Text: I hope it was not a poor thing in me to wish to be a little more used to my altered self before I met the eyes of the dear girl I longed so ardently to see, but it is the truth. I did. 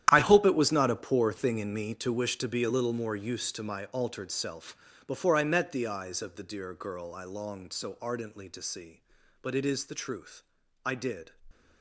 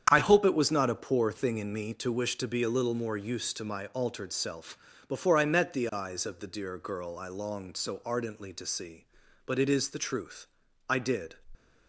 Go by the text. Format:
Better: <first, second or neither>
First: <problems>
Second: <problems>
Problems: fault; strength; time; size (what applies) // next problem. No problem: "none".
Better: second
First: gets quieter; strong; throughout; 14.5 dB // starts louder than the rest; strong; until 1.1 s; 11 dB // pauses between "self" and "before"; slight; at 4.7 s; 0.32 s long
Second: starts louder than the rest; strong; until 1.1 s; 8.5 dB // pauses between "self" and "before"; slight; at 4.7 s; 0.32 s long